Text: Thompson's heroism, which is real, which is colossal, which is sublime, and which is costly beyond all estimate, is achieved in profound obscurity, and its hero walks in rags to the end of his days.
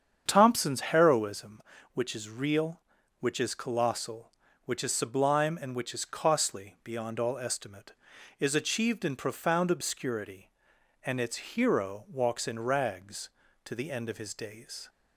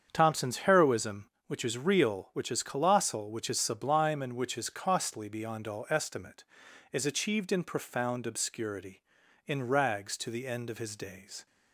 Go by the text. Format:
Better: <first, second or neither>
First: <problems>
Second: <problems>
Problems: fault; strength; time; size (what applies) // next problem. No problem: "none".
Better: first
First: starts louder than the rest; strong; until 1.2 s; 8 dB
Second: starts louder than the rest; strong; until 1.1 s; 7.5 dB // skips "and its hero walks"; at 9.2 s